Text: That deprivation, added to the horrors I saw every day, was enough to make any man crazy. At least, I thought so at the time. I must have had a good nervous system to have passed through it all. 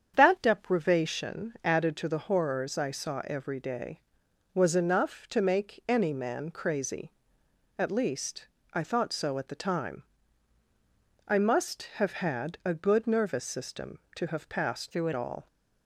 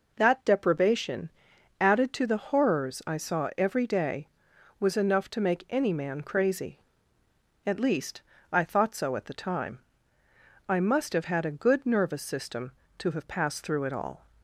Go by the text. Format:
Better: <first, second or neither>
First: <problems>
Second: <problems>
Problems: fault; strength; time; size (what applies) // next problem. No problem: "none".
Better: second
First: starts louder than the rest; strong; until 1.1 s; 8 dB // changes voice from "through" to "it"; from 14.9 to 15.1 s; 0.2 s long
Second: none